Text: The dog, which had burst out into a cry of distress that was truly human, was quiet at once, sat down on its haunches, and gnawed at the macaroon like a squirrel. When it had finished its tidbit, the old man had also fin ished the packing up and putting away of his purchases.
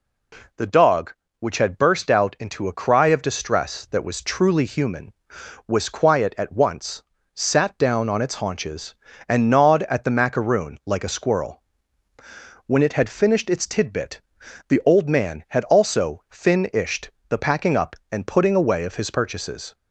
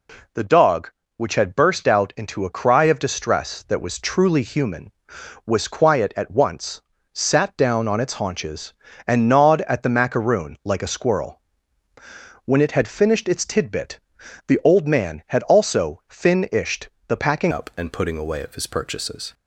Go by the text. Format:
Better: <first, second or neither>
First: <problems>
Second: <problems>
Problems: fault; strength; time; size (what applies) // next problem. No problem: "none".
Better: first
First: pauses between "ished" and "the"; slight; at 17.0 s; 0.18 s long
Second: pauses between "ished" and "the"; slight; at 16.8 s; 0.18 s long // changes voice at "up"; from 17.5 s on; 1.8 s long